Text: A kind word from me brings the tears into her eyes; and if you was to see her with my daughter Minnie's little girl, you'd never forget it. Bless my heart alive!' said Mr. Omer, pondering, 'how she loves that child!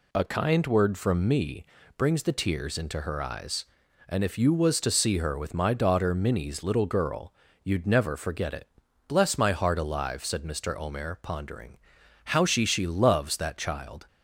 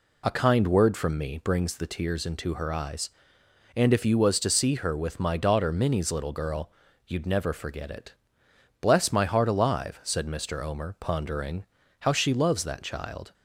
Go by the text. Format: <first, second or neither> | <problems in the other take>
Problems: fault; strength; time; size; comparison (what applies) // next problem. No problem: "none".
second | pauses between "me" and "brings"; slight; at 1.6 s; 0.34 s long // says "she" twice; at 12.6 s